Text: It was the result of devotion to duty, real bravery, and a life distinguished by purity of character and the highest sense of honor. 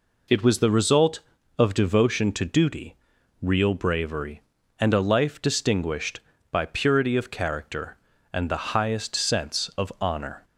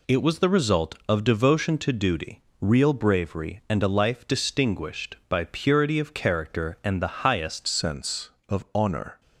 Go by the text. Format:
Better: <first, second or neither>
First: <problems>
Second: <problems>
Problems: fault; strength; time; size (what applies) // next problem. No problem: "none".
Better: first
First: none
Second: changes voice at "sense"; from 7.6 s on; 1.6 s long